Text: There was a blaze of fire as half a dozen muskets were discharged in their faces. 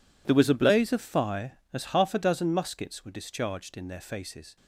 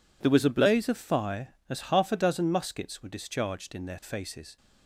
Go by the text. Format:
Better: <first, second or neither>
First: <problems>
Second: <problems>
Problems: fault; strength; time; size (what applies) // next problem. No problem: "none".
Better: second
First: gets quieter; strong; throughout; 16.5 dB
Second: none